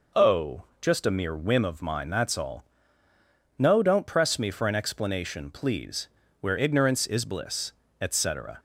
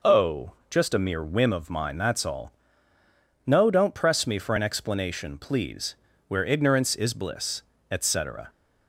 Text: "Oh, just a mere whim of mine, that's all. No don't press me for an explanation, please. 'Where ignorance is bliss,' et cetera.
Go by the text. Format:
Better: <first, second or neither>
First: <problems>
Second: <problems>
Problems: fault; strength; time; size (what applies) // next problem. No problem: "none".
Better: neither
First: none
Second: none